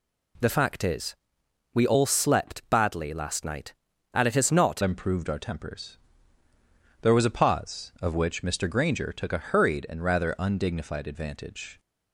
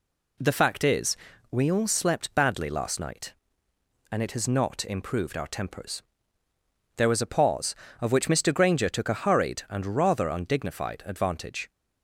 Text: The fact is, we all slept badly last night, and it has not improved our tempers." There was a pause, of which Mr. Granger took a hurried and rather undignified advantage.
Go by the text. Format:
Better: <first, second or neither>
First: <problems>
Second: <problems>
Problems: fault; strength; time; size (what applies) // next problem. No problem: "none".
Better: second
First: changes voice at "improved"; from 4.8 s on; 6.9 s long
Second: none